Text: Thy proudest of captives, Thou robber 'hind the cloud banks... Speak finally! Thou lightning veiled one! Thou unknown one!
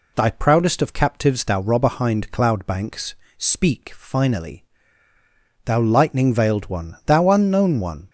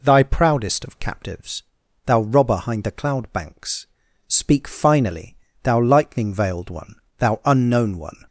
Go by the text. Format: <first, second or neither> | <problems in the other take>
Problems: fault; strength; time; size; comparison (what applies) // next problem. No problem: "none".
second | skips "the"; at 2.3 s